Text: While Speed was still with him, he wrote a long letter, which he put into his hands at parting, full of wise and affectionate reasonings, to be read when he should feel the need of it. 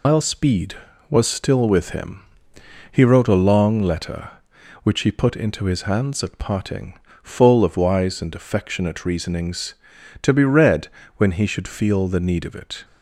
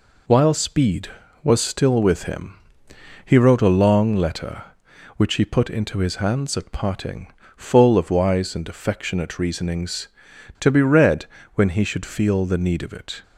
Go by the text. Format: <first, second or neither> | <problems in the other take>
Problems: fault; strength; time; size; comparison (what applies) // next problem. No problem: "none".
second | loses the start of "While"; at 0.0 s; 95 ms // pauses between "read" and "when"; slight; at 10.8 s; 0.30 s long; slight in the second